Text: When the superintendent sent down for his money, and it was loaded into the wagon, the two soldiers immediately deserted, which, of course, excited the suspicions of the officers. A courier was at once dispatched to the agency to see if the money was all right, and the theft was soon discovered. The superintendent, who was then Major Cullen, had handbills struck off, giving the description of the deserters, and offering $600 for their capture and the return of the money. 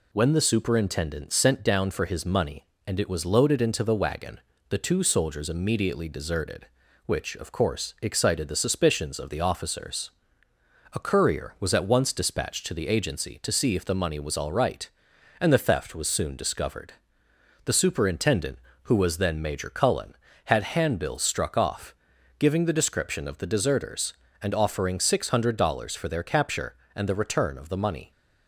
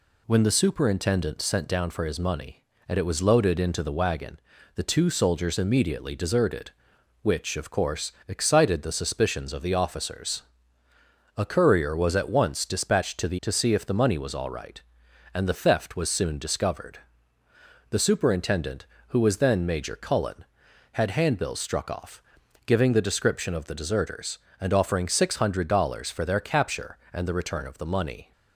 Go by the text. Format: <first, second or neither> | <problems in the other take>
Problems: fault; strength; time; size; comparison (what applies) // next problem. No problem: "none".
first | skips "agency"; at 13.4 s